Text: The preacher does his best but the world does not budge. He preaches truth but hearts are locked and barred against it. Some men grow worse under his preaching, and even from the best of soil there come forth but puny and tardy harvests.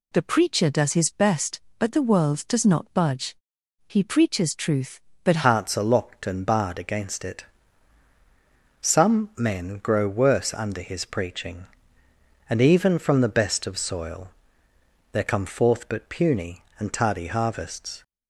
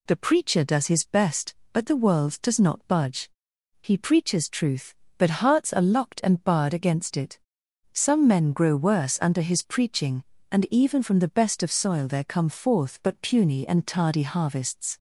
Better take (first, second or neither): second